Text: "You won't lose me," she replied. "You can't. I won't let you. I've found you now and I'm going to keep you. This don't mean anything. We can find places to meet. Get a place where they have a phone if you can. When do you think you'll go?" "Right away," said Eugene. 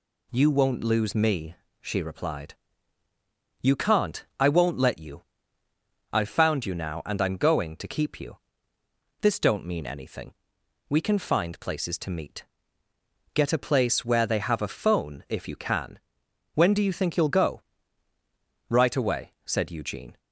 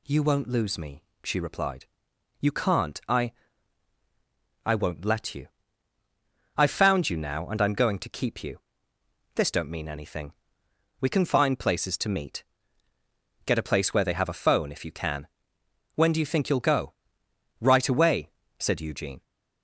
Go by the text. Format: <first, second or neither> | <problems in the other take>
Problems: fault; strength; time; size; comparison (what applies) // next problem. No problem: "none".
first | says "I" twice; at 4.6 s